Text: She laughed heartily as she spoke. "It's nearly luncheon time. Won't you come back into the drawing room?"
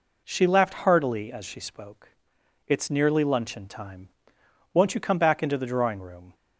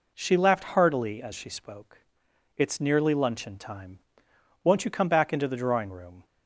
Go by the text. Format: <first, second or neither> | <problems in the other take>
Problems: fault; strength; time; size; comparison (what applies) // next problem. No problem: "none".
neither | none